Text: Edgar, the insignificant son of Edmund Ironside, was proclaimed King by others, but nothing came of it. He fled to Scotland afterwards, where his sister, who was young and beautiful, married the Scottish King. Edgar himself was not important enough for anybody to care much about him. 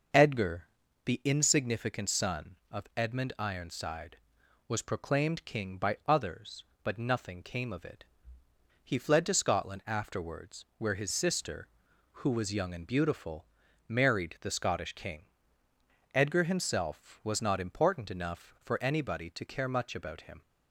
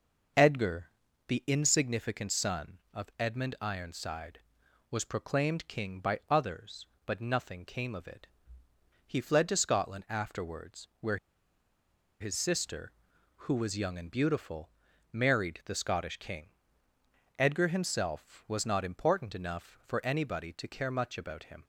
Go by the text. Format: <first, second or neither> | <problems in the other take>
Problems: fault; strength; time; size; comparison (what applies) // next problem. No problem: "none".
first | starts louder than the rest; until 1.7 s; 6 dB; also in the first // pauses between "where" and "his"; at 11.1 s; 1.0 s long